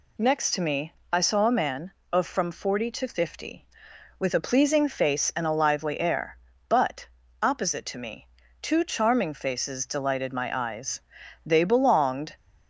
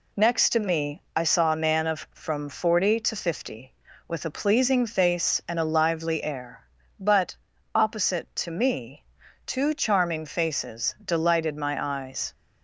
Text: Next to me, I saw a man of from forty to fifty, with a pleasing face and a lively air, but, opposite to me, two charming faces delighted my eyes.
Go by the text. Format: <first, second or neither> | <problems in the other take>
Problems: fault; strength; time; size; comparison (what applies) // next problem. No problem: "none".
second | goes on to say "They belonged"; noticeable; from 11.4 s on; 0.88 s long